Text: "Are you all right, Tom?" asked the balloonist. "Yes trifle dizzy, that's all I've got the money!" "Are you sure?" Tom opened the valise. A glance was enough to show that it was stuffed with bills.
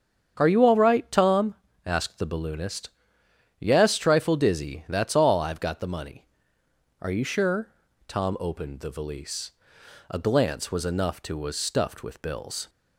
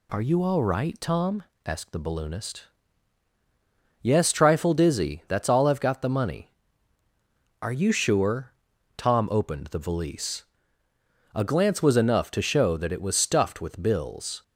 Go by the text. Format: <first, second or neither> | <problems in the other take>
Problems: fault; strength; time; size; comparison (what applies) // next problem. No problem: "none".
second | starts louder than the rest; strong; until 1.3 s; 7.5 dB // skips "show that it"; at 11.3 s